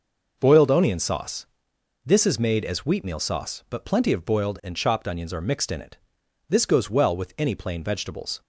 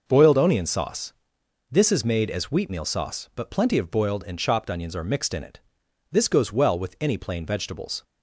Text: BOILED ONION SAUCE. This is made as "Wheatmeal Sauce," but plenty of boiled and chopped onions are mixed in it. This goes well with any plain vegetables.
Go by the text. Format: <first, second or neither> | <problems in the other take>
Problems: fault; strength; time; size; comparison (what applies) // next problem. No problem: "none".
neither | none